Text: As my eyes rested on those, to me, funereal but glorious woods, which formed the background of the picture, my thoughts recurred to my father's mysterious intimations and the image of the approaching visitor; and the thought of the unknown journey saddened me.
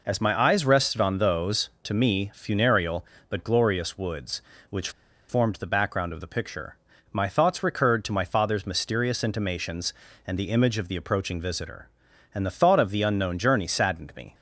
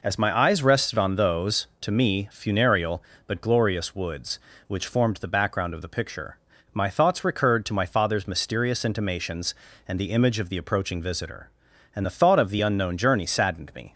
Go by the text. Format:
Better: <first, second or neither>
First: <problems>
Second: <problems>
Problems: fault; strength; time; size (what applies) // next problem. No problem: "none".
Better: second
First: pauses between "which" and "formed"; at 4.8 s; 0.39 s long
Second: none